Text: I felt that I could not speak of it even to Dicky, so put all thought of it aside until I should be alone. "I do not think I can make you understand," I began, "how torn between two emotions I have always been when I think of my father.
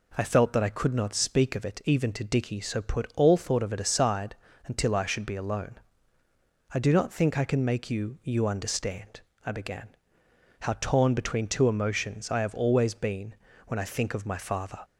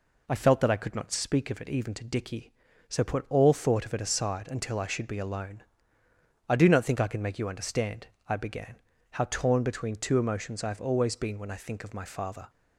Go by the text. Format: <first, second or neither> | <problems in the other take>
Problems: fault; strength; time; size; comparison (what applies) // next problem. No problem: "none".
second | pauses between "aside" and "until"; slight; at 4.3 s; 0.32 s long // says "you" twice; at 8.2 s // pauses between "been" and "when"; slight; at 13.3 s; 0.32 s long